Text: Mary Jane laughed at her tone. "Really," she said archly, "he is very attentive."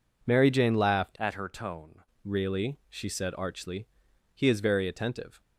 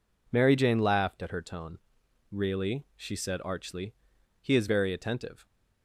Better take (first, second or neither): second